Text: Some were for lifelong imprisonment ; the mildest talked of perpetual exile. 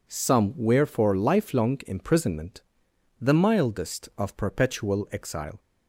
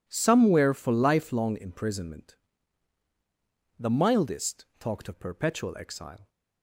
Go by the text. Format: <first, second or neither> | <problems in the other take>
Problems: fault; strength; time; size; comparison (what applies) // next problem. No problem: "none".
second | skips "talked"; at 4.1 s